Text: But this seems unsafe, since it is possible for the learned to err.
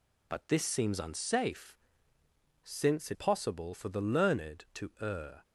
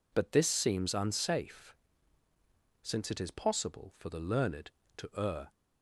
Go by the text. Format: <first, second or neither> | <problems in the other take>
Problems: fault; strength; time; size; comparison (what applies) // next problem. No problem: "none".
second | skips "is"; at 3.1 s